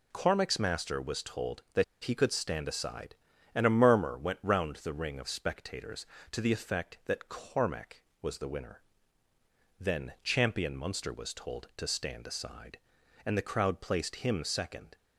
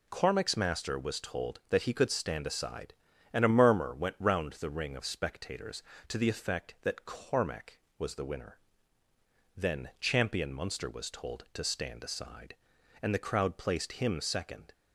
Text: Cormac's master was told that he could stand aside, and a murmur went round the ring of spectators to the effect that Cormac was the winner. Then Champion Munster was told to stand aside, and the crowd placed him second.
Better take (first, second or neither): second